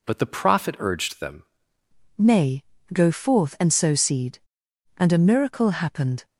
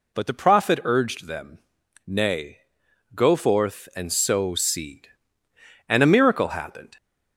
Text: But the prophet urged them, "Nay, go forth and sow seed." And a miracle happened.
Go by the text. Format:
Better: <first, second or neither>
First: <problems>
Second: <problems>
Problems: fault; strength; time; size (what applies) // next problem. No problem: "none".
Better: second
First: changes voice at "Nay"; from 2.1 s on; 4.1 s long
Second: none